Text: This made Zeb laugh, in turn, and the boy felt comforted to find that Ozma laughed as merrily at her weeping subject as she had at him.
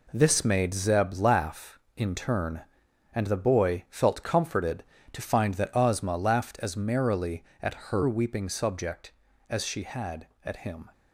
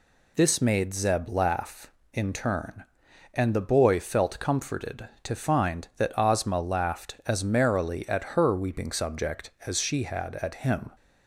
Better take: second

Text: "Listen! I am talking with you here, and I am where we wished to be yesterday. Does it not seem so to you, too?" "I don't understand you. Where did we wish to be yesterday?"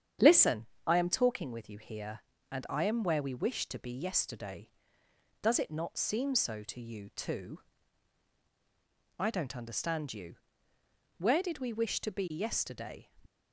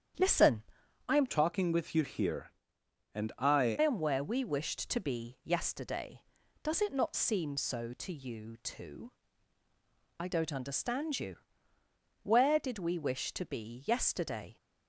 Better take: first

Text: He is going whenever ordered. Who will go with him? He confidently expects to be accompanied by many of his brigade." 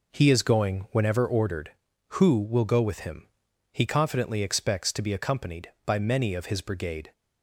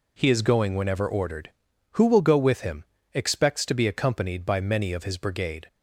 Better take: first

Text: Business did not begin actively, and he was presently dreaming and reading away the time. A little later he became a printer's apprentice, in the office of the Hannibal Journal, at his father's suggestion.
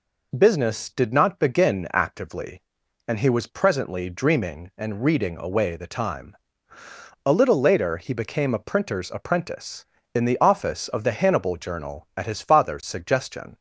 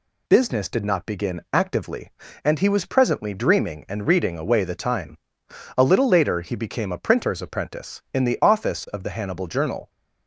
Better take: first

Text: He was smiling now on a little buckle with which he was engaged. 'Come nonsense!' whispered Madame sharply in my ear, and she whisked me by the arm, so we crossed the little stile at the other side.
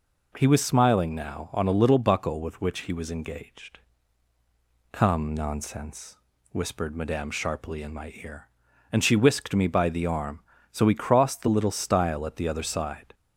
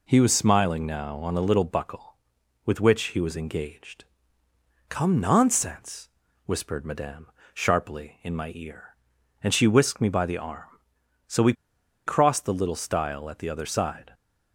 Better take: first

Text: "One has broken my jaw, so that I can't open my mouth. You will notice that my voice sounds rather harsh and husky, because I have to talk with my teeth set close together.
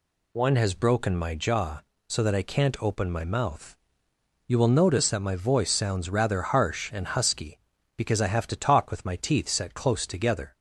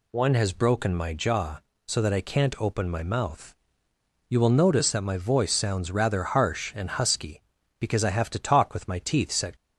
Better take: first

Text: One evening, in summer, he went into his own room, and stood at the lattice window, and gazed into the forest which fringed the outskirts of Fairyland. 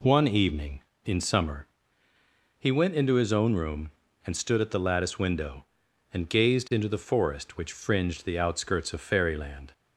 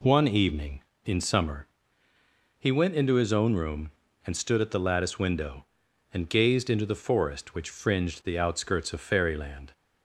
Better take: neither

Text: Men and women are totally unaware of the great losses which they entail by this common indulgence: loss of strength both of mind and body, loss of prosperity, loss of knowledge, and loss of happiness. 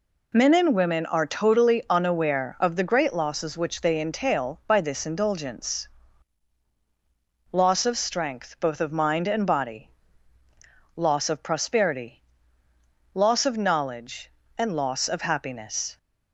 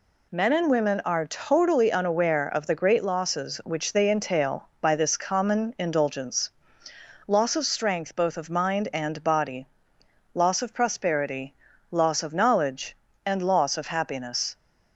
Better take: second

